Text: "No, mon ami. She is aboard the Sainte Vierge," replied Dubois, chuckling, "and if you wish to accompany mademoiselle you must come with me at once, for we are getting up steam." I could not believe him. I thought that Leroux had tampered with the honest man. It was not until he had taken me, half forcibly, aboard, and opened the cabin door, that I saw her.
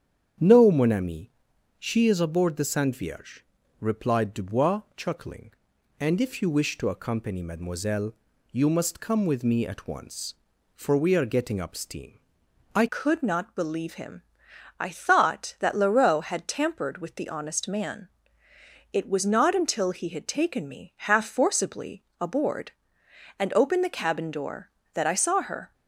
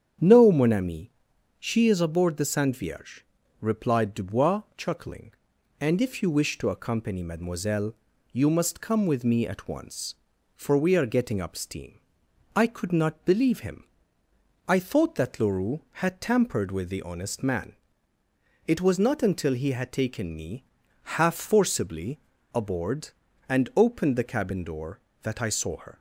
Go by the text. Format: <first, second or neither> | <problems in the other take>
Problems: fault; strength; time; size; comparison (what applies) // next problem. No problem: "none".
second | starts louder than the rest; strong; until 1.8 s; 8.5 dB; strong in the second // pauses between "mademoiselle" and "you"; at 8.1 s; 0.38 s long; also in the second // changes voice at "could"; from 12.8 s on; 12.9 s long